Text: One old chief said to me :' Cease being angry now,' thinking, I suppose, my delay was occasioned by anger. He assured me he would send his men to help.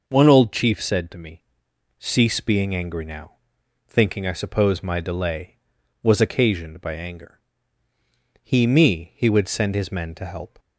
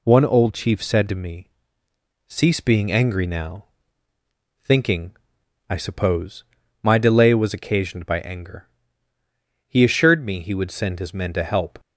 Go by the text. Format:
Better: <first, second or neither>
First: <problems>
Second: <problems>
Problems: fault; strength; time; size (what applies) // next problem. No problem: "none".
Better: second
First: skips "assured"; at 8.6 s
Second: none